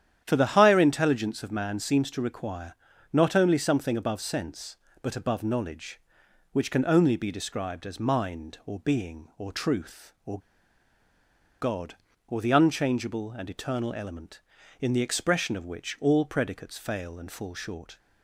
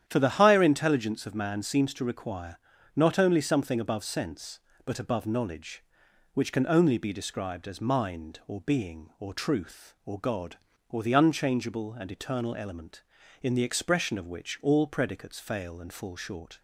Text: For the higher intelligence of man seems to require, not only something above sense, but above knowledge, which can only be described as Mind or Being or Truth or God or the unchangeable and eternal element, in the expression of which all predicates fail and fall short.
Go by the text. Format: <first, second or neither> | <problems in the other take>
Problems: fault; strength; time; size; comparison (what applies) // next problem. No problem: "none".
second | starts louder than the rest; strong; until 1.2 s; 10 dB; strong in the second // pauses between "or" and "God"; at 10.3 s; 1.2 s long